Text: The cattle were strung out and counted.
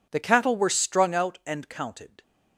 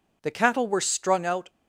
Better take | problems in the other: first | stops before "and counted"; at 1.4 s

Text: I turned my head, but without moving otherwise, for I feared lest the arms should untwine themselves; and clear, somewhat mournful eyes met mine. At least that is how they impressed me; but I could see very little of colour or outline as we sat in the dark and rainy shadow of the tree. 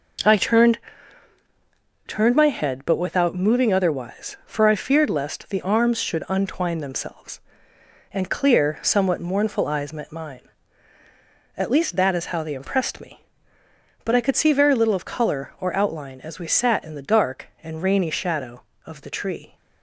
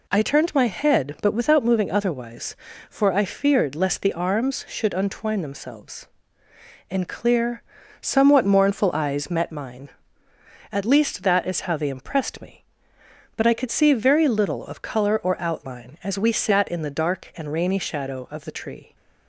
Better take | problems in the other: second | says "turned" twice; at 2.0 s

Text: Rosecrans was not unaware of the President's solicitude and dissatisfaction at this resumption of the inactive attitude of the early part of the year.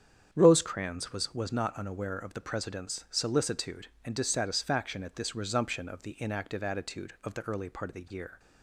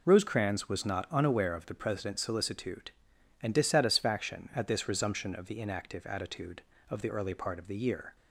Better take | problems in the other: second | starts louder than the rest; strong; until 1.3 s; 8 dB // says "was" twice; at 1.3 s

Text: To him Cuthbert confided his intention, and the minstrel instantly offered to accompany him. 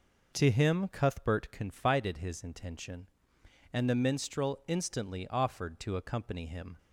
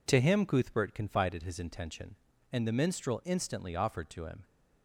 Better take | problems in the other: first | skips "accompany"; at 4.2 s

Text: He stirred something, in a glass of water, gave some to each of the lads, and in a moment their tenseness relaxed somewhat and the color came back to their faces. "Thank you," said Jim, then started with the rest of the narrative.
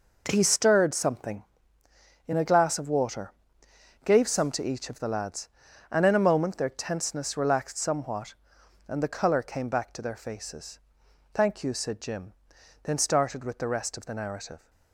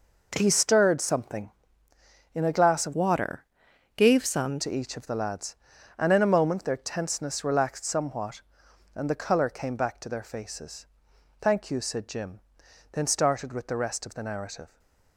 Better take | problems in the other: first | changes voice from "water" to "some"; from 2.9 to 4.6 s; 1.7 s long // stays silent after the last word; slight; from 14.6 s on; 0.5 s long

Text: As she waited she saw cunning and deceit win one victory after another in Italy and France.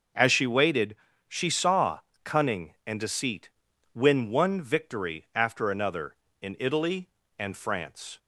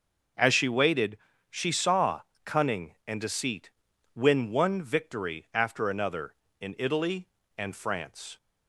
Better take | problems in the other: neither | pauses between "waited" and "she"; slight; the same in both // pauses between "saw" and "cunning"; slight; the same in both // pauses between "deceit" and "win"; noticeable; the same in both

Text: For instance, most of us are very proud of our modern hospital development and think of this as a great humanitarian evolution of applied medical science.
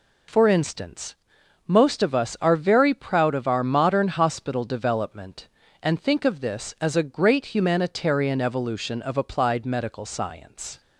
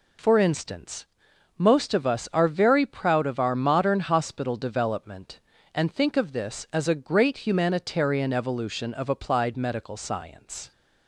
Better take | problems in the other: neither | none

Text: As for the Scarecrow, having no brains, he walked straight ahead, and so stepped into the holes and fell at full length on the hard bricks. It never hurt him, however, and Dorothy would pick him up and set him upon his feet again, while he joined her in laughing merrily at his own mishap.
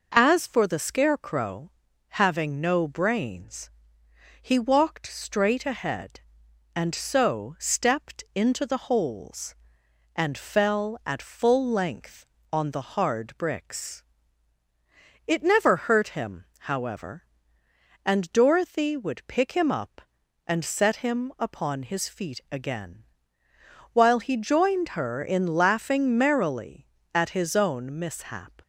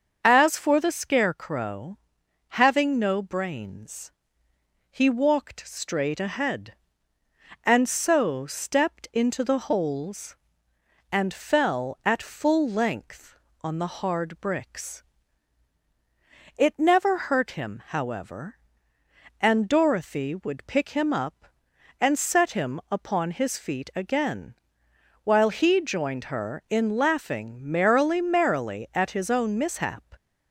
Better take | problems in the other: first | starts louder than the rest; until 1.2 s; 6.5 dB // says "merrily" twice; at 28.2 s

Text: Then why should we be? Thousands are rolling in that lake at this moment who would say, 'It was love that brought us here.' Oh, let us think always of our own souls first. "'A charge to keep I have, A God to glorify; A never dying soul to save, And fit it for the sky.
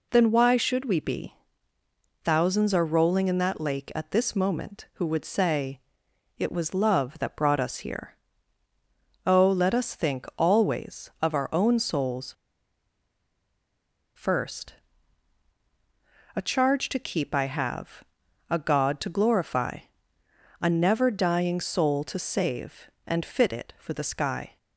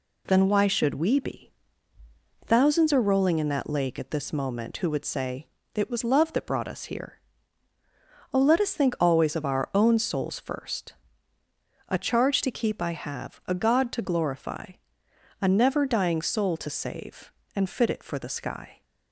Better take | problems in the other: second | pauses between "souls" and "first"; strong; at 12.3 s; 1.8 s long

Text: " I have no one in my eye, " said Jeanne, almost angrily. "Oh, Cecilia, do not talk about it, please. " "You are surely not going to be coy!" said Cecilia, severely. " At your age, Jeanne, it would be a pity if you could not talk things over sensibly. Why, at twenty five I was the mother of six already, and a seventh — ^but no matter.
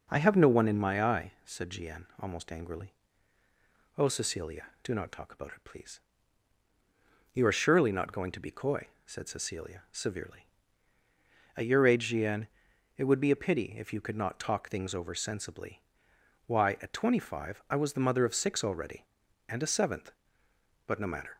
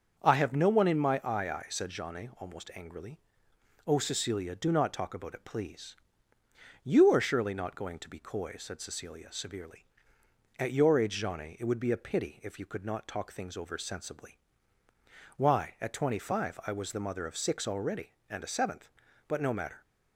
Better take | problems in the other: first | starts louder than the rest; until 1.2 s; 6.5 dB; strong in the first // says "eye" twice; at 1.4 s

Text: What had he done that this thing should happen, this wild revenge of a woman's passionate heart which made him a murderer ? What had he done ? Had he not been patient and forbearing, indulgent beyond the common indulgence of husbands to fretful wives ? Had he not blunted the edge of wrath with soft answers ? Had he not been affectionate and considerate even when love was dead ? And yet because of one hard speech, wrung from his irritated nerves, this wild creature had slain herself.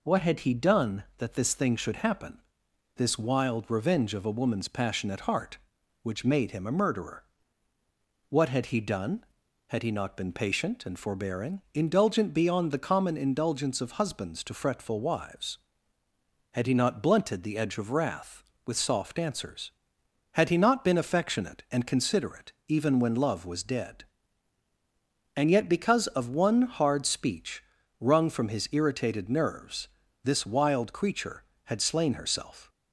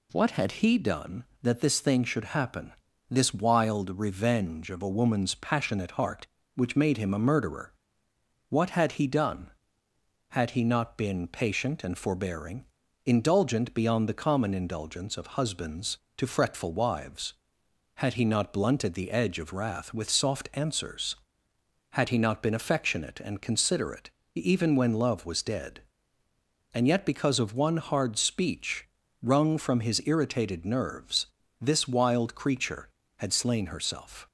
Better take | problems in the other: neither | pauses between "considerate" and "even"; slight; the same in both

